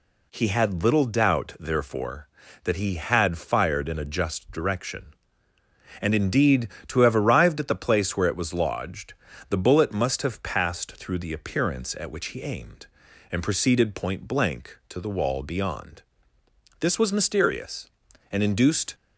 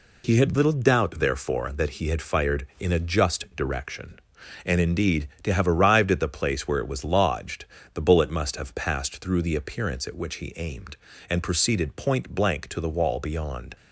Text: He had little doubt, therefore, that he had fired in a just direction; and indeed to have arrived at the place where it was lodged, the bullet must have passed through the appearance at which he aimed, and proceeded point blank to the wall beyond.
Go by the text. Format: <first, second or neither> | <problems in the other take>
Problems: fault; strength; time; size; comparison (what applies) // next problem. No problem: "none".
second | goes on to say "This was mysterious and induced"; strong; from 16.7 s on; 2.1 s long